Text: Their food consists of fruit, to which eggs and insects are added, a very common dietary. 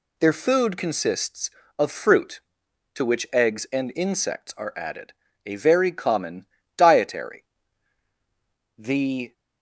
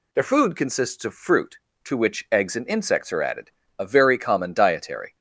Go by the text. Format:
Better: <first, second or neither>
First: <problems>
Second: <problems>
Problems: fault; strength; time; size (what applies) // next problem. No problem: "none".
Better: second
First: pauses between "common" and "dietary"; slight; at 6.4 s; 0.32 s long // goes on to say "The"; from 8.7 s on; 0.56 s long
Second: none